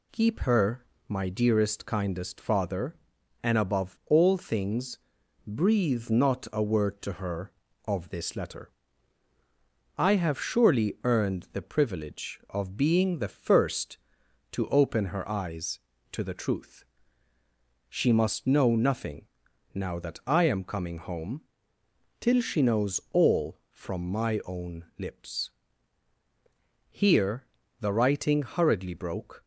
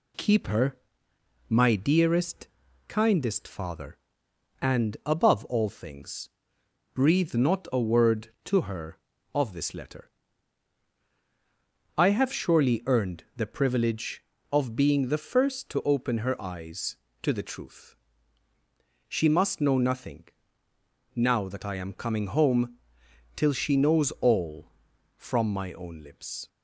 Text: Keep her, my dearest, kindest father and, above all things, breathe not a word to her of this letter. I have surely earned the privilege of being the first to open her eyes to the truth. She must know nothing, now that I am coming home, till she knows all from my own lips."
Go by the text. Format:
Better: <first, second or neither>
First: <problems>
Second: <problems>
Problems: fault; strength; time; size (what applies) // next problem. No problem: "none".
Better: second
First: goes on to say "Here the writing hurriedly broke"; strong; from 26.9 s on; 2.5 s long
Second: none